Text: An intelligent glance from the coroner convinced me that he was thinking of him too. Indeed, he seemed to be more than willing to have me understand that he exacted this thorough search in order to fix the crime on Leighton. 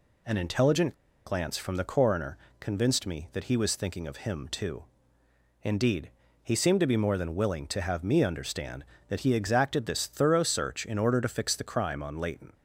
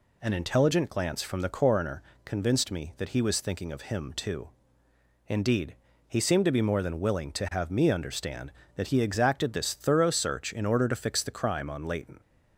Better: second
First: pauses between "intelligent" and "glance"; slight; at 0.9 s; 0.32 s long // pauses between "coroner" and "convinced"; slight; at 2.3 s; 0.24 s long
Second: pauses between "coroner" and "convinced"; slight; at 2.0 s; 0.24 s long

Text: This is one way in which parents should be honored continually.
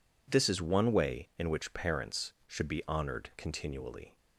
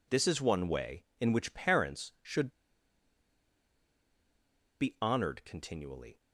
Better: first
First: none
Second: pauses between "should" and "be"; strong; at 2.4 s; 2.3 s long

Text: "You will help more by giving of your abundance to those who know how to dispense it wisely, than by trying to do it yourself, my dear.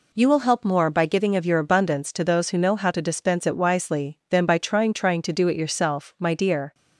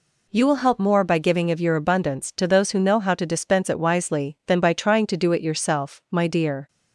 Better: second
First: says "trying" twice; at 4.9 s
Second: none

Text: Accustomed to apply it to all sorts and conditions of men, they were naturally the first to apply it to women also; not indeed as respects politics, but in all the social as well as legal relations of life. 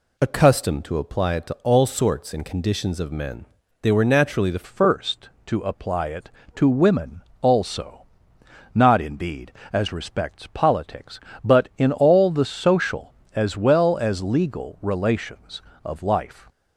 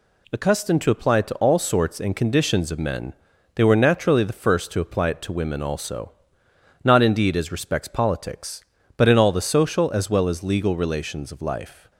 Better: second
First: changes voice at "first"; from 4.6 s on; 11.8 s long // pauses between "women" and "also"; slight; at 7.2 s; 0.22 s long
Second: none

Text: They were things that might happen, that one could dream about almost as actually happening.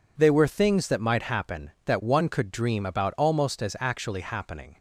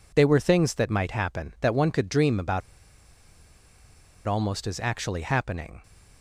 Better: first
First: none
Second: pauses between "about" and "almost"; strong; at 2.6 s; 1.6 s long

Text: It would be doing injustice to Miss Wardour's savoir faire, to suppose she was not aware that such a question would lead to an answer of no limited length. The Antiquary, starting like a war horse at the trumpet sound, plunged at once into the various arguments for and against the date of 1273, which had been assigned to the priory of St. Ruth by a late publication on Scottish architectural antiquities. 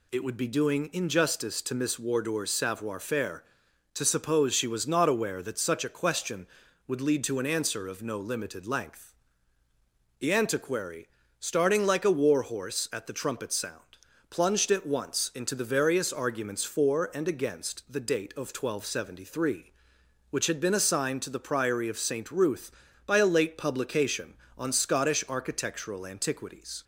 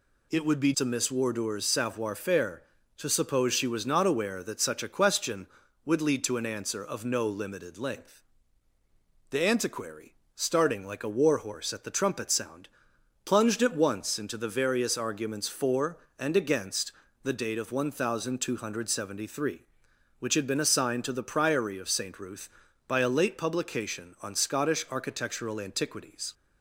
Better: first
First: none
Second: skips "doing injustice"; at 0.7 s // pauses between "against" and "the"; slight; at 16.9 s; 0.32 s long

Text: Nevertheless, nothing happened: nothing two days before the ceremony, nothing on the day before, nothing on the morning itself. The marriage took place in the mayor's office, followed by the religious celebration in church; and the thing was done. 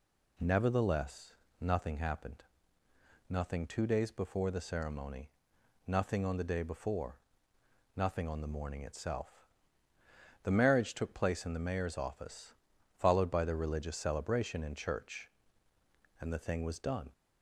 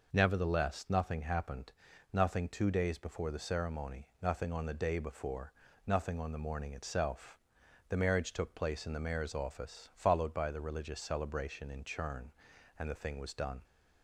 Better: first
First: none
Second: says "churn" for "church"; at 11.8 s

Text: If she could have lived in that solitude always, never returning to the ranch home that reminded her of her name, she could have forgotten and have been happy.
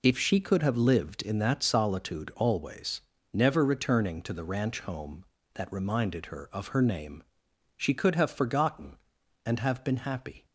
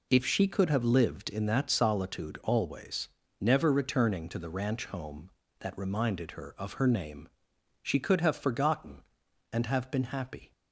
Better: neither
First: none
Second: none

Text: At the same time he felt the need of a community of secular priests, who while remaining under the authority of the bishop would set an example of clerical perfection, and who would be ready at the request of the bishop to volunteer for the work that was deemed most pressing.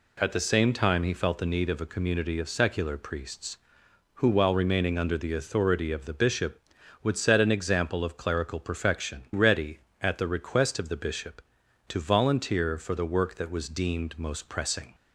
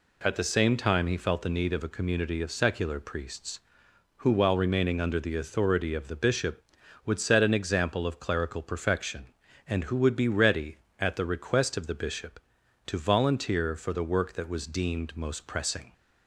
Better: second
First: skips "and who would be"; at 9.3 s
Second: none

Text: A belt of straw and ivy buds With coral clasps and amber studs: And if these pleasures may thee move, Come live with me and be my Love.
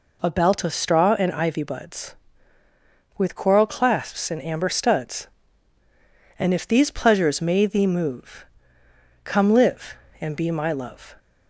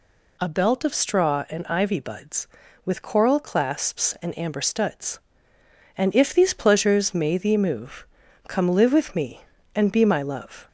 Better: second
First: skips "with me"; at 10.0 s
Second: none

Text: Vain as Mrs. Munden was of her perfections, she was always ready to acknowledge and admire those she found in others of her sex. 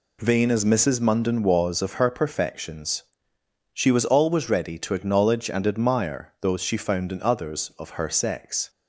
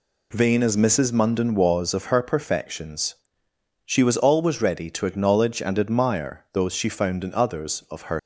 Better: first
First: none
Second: stops before "sex"; at 8.1 s

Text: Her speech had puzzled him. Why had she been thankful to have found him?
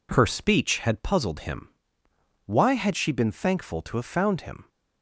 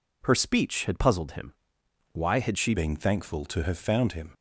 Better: first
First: none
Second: changes voice at "been"; from 2.7 s on; 1.6 s long

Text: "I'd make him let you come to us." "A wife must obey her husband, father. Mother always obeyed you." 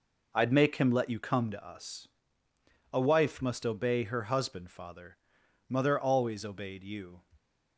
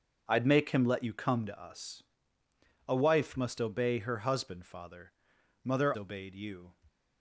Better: first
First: none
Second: starts louder than the rest; until 1.2 s; 6 dB // skips "always"; at 5.9 s

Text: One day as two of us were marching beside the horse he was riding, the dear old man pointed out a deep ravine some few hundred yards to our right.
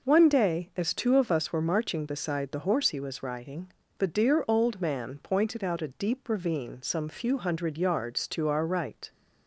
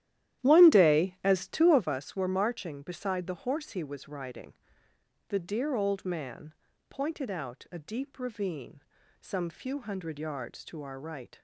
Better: first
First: none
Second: starts louder than the rest; strong; until 1.9 s; 12.5 dB // pauses between "man" and "pointed"; slight; at 6.5 s; 0.34 s long // pauses between "ravine" and "some"; at 8.7 s; 0.40 s long

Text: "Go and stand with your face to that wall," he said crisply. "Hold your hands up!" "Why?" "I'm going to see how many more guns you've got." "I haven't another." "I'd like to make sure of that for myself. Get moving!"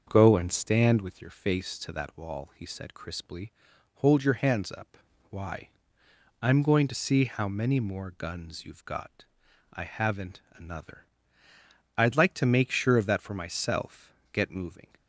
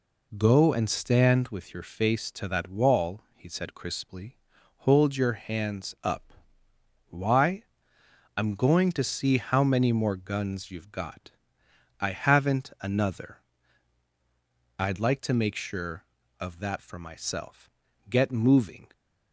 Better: second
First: starts louder than the rest; until 1.4 s; 6.5 dB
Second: none

